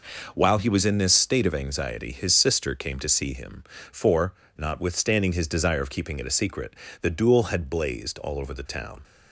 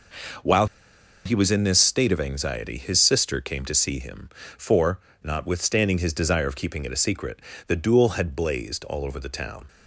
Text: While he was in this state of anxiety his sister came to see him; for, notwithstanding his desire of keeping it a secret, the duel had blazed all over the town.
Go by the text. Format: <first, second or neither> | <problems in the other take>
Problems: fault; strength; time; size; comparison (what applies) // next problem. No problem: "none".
first | pauses between "While" and "he"; noticeable; at 0.6 s; 0.59 s long